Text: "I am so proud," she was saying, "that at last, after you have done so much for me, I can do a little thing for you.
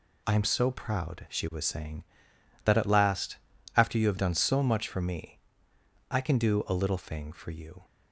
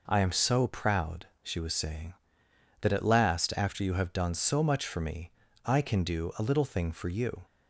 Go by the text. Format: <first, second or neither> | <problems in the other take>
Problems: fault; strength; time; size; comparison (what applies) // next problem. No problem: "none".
neither | none